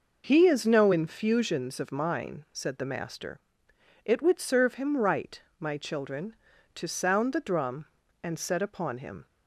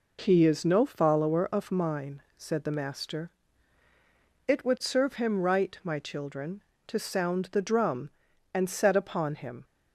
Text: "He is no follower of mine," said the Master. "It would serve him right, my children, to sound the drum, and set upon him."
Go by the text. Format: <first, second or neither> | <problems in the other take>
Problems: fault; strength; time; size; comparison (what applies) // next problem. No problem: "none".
second | says "infusions" for "follower"; at 0.9 s